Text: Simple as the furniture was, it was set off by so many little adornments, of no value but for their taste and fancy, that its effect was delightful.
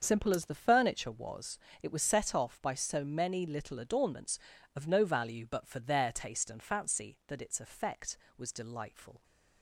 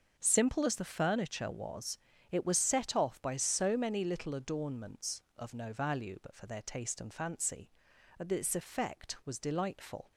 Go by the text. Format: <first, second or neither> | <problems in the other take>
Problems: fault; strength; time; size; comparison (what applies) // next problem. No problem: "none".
neither | starts louder than the rest; the same in both